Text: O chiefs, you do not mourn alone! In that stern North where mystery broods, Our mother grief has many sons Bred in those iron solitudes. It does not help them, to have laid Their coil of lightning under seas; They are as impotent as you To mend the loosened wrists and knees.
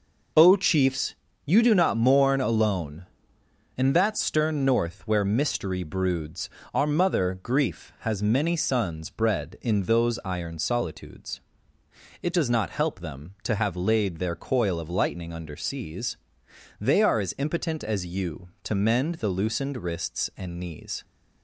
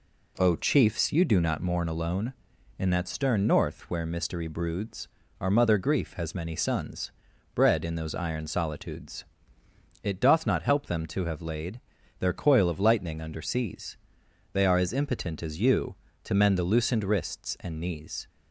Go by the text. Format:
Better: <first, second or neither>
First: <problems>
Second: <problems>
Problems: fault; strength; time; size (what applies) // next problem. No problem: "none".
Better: first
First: none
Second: pauses between "sons" and "Bred"; at 7.1 s; 0.44 s long // says "doth" for "does"; at 10.2 s // pauses between "laid" and "Their"; at 11.8 s; 0.38 s long